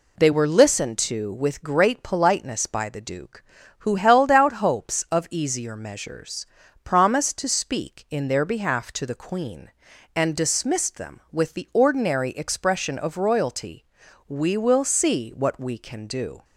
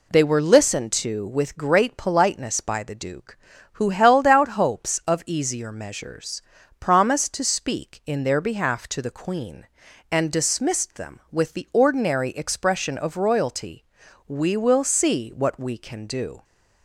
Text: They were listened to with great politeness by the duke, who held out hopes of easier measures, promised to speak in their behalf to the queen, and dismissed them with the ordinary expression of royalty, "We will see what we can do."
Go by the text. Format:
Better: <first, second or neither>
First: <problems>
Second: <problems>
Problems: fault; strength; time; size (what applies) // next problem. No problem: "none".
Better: neither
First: none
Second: none